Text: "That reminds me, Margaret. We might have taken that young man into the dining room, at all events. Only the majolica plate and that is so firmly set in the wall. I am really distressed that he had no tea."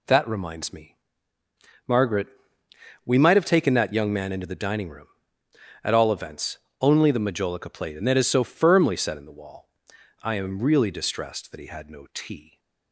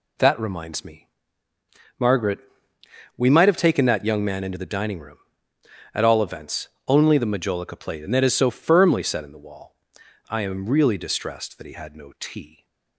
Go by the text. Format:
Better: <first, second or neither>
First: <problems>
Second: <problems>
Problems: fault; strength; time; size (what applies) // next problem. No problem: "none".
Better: neither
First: none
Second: none